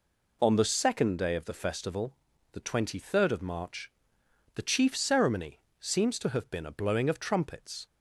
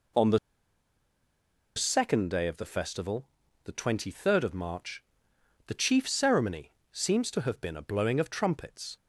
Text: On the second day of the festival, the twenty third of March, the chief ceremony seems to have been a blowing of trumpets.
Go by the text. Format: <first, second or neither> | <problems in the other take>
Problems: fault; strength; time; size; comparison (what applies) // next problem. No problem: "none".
first | pauses between "the" and "second"; strong; at 0.3 s; 1.3 s long // pauses between "ceremony" and "seems"; slight; at 6.7 s; 0.20 s long; slight in the first